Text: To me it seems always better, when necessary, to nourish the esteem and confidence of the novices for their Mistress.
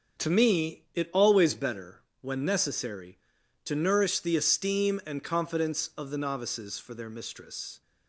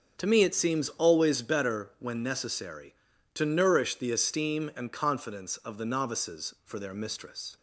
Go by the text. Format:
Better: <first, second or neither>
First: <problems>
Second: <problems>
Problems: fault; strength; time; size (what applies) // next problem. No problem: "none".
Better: second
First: starts louder than the rest; until 1.3 s; 6.5 dB // skips "seems"; at 1.1 s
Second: starts louder than the rest; strong; until 1.2 s; 7 dB